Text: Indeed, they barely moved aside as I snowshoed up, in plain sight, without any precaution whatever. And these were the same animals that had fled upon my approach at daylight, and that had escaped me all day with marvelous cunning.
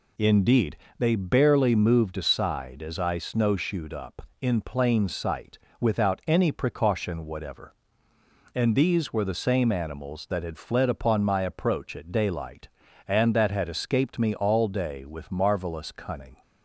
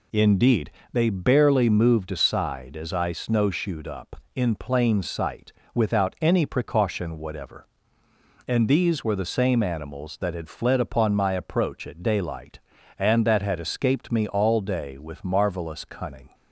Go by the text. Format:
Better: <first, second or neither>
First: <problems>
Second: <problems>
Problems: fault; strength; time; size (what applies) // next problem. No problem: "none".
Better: neither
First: none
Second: none